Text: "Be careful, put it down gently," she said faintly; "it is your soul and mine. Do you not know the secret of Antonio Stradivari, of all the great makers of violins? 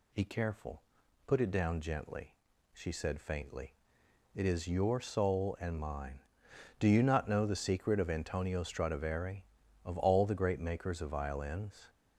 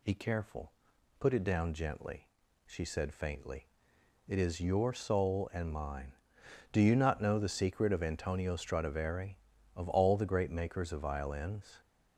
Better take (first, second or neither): neither